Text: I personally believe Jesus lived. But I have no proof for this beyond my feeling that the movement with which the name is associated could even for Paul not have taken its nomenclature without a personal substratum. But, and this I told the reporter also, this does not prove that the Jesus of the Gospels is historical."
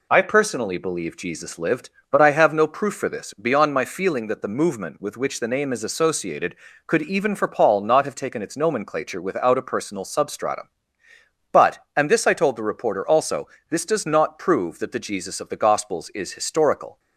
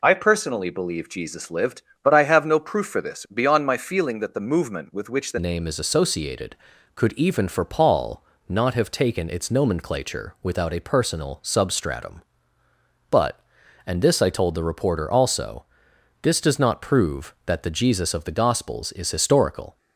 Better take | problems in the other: first | changes voice at "name"; from 5.3 s on; 14.4 s long // pauses between "Paul" and "not"; slight; at 8.2 s; 0.26 s long

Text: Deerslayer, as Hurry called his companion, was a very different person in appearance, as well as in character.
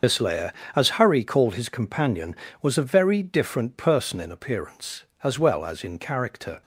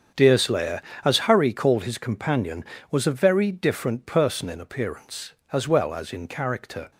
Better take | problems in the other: second | loses the start of "Deerslayer"; at 0.0 s; 175 ms // starts louder than the rest; until 1.2 s; 6 dB; strong in the second

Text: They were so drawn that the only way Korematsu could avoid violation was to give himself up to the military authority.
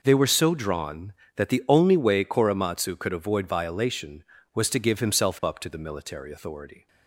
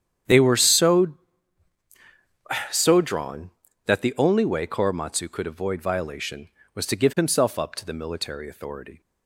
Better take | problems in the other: first | starts louder than the rest; strong; until 2.8 s; 9 dB // says "so" twice; at 2.7 s

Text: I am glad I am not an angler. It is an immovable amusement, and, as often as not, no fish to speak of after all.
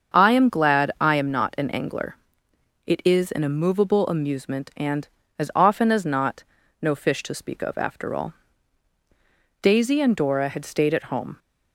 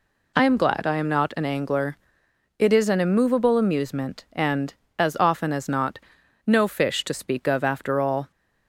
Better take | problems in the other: second | starts louder than the rest; until 1.2 s; 7 dB // goes on to say "Daisy and Dora had stayed at home"; strong; from 9.6 s on; 1.7 s long

